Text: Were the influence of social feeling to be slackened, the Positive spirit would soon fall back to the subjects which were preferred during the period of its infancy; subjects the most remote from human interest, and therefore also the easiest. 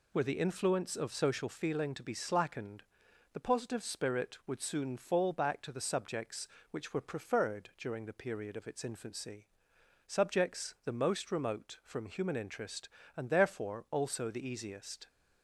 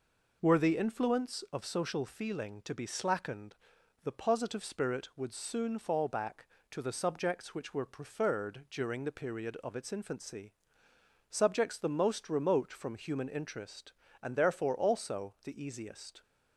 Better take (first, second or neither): neither